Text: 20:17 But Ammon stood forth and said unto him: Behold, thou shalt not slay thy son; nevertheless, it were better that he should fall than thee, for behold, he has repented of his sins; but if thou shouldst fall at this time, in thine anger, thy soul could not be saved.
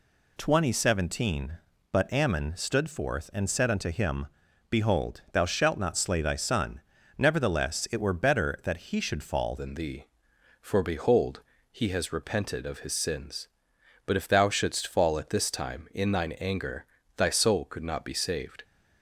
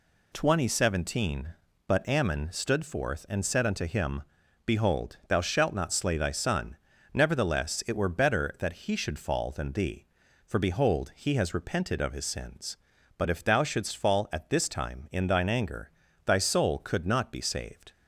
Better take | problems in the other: second | changes voice at "than"; from 9.5 s on; 9.1 s long

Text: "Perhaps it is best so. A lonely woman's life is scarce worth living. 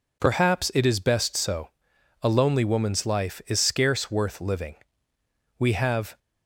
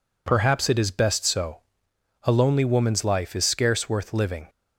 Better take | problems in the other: second | goes on to say "We have"; from 5.6 s on; 0.58 s long

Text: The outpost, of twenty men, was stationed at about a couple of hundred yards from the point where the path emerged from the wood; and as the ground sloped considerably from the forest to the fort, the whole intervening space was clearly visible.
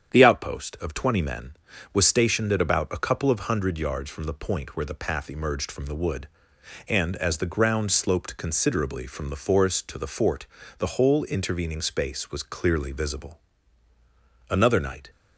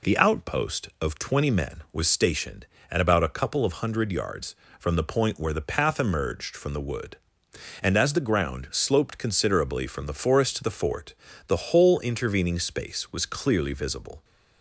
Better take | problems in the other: second | starts louder than the rest; strong; until 1.1 s; 8.5 dB // goes on to say "Another night"; noticeable; from 14.4 s on; 0.62 s long

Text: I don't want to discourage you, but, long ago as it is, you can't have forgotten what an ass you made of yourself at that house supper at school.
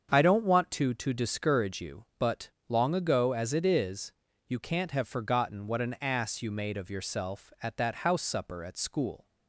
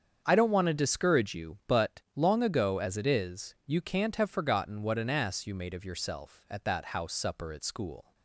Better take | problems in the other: second | starts louder than the rest; strong; until 1.1 s; 7 dB; strong in the second // says "to" twice; at 0.9 s

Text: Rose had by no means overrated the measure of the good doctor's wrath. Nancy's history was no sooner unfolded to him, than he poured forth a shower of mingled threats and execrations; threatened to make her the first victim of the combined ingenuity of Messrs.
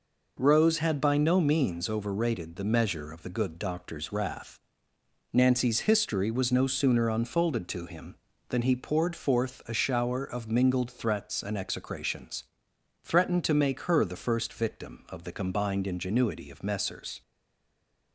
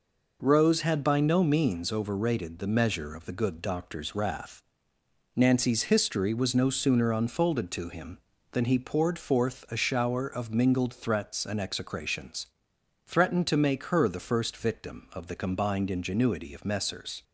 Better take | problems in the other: second | stays silent after the last word; slight; from 17.2 s on; 0.9 s long

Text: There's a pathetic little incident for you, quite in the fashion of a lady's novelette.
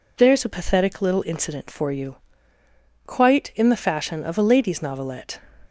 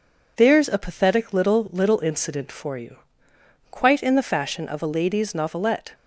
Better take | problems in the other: first | says "little" twice; at 1.7 s

